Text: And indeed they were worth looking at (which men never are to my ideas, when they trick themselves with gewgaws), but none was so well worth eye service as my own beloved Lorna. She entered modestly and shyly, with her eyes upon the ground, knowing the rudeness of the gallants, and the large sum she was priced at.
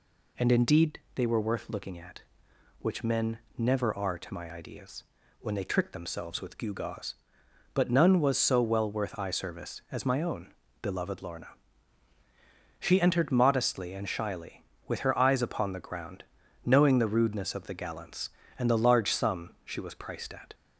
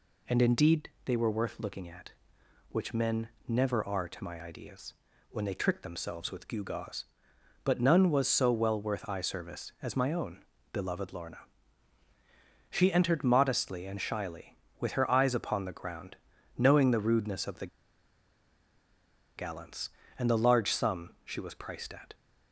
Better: first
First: pauses between "indeed" and "they"; slight; at 0.9 s; 0.16 s long // pauses between "men" and "never"; slight; at 3.3 s; 0.18 s long // pauses between "own" and "beloved"; slight; at 10.5 s; 0.30 s long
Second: pauses between "indeed" and "they"; slight; at 0.8 s; 0.16 s long // pauses between "men" and "never"; slight; at 3.2 s; 0.18 s long // pauses between "own" and "beloved"; slight; at 10.4 s; 0.30 s long // pauses between "the" and "gallants"; strong; at 17.6 s; 1.7 s long

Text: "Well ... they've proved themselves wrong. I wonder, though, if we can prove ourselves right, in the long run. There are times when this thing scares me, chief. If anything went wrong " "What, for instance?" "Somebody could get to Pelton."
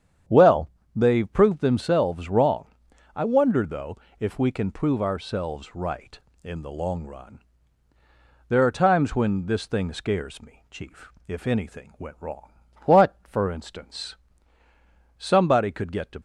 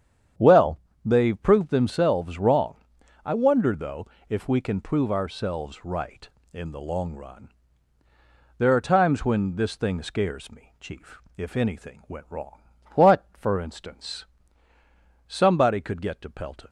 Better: second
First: starts louder than the rest; strong; until 1.5 s; 8.5 dB // stops before "Pelton"; at 16.1 s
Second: starts louder than the rest; strong; until 1.6 s; 8.5 dB

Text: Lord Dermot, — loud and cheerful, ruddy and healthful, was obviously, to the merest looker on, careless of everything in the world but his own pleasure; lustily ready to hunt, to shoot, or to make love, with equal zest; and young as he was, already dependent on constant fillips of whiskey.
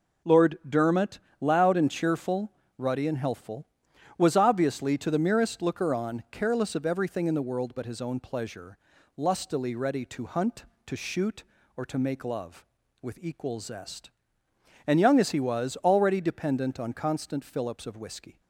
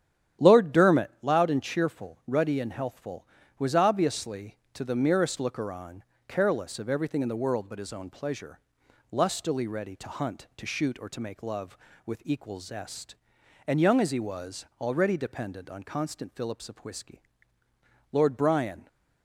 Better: first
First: none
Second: starts louder than the rest; strong; until 1.5 s; 10.5 dB // goes on to say "Lord Brian"; noticeable; from 18.1 s on; 0.76 s long

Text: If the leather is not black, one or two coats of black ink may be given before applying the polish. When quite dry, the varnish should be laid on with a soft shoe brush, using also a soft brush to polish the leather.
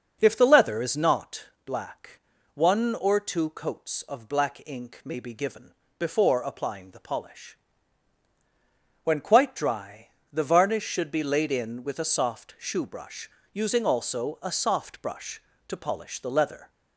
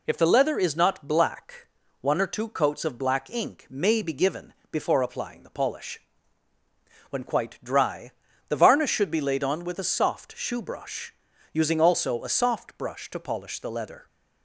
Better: second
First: starts louder than the rest; noticeable; until 1.2 s; 6 dB // pauses between "not" and "black"; slight; at 1.4 s; 0.20 s long // pauses between "given" and "before"; slight; at 5.7 s; 0.22 s long // says "in" for "on"; at 11.5 s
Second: pauses between "given" and "before"; slight; at 4.5 s; 0.16 s long

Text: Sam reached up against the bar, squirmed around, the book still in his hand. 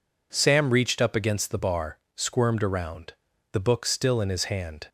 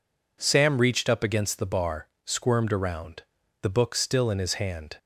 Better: neither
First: none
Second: none

